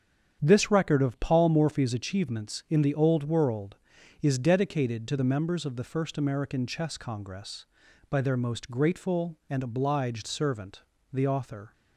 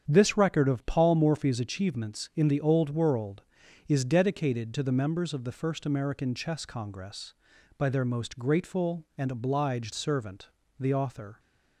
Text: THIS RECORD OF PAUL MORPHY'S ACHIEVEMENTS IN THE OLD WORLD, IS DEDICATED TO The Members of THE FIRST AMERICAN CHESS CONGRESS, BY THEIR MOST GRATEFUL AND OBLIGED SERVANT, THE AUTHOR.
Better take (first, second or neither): neither